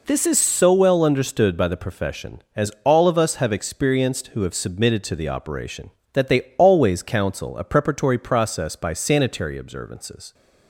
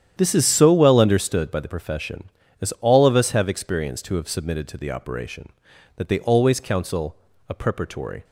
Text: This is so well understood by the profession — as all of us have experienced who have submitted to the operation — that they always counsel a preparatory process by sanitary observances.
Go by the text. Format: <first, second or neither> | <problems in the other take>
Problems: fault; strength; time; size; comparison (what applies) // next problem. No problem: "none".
first | starts louder than the rest; strong; until 1.1 s; 9.5 dB // pauses between "counsel" and "a"; slight; at 7.1 s; 0.34 s long // stops before "process by sanitary observances"; at 8.2 s